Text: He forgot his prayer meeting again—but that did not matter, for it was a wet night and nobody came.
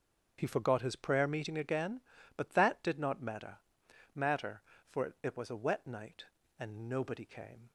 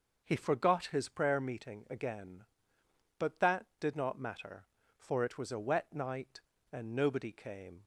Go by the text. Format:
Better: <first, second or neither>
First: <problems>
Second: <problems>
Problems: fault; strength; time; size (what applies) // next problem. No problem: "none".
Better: second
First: starts louder than the rest; strong; until 1.4 s; 7.5 dB // says "matter" twice; at 4.1 s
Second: none